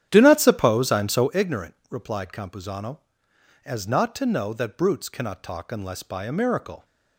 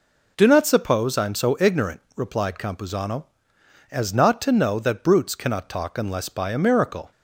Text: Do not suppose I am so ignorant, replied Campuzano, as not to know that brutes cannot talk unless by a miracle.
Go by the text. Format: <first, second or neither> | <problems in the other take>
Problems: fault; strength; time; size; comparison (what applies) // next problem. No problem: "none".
second | starts louder than the rest; strong; until 1.3 s; 11 dB